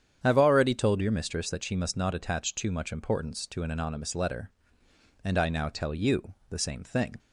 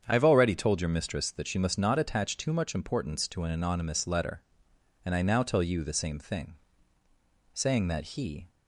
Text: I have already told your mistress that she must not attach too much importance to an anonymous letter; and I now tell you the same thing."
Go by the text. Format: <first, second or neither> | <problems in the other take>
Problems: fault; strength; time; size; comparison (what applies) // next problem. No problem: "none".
first | starts louder than the rest; strong; until 1.0 s; 7.5 dB; strong in the first // goes on to say "Saying that he"; noticeable; from 7.5 s on; 0.96 s long